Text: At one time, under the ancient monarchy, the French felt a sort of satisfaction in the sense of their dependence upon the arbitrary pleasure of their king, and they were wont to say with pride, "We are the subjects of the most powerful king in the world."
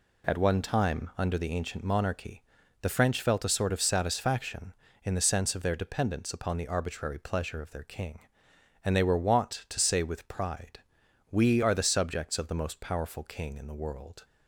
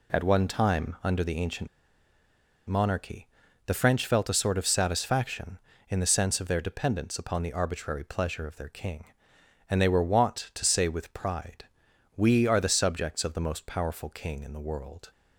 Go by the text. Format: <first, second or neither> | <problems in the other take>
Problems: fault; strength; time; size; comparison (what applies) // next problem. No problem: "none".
first | pauses between "ancient" and "monarchy"; at 1.6 s; 1.0 s long